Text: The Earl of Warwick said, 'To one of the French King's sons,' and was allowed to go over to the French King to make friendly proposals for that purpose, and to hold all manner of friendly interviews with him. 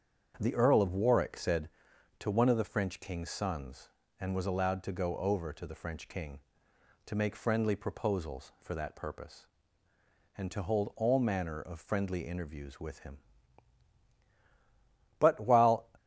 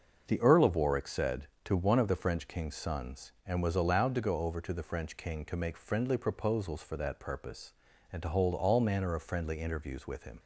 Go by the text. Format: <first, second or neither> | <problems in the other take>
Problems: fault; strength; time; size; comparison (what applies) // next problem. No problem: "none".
second | starts louder than the rest; strong; until 1.4 s; 7.5 dB; also in the second // goes on to say "But while"; noticeable; from 15.1 s on; 0.70 s long